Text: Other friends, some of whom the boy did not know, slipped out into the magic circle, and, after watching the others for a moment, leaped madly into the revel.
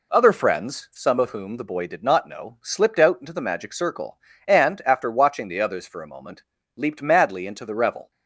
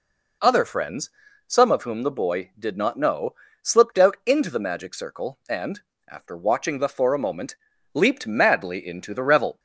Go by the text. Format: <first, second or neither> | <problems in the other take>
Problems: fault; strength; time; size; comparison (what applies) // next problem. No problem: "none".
first | skips "others"; at 6.8 s